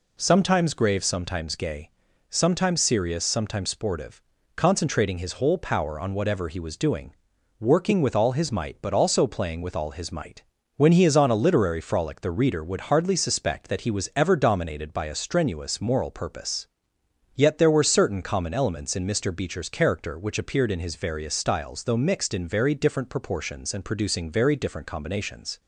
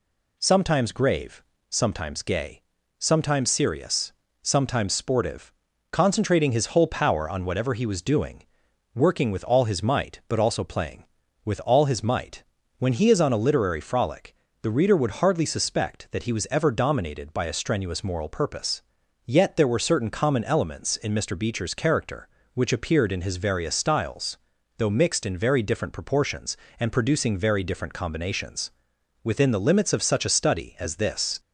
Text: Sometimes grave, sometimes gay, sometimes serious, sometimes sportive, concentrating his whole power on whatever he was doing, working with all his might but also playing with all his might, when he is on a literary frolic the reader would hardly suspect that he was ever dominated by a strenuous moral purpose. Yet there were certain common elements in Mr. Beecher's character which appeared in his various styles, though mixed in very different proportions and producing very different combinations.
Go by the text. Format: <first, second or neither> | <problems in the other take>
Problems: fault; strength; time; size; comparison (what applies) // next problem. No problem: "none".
first | pauses between "frolic" and "the"; slight; at 14.3 s; 0.26 s long // goes on to say "Within the limits of such a study as this"; strong; from 29.2 s on; 2.1 s long